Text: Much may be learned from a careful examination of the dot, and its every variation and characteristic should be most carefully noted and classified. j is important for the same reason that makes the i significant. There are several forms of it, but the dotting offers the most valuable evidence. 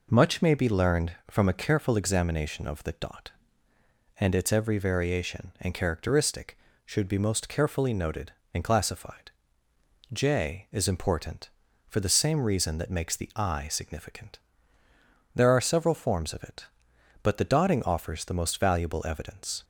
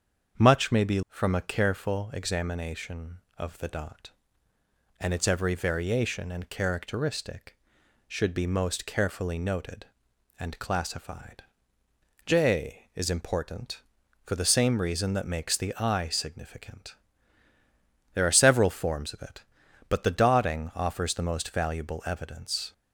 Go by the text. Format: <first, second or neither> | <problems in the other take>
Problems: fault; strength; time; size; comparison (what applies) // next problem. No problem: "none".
first | starts louder than the rest; strong; until 1.4 s; 7.5 dB // skips "learned"; at 1.0 s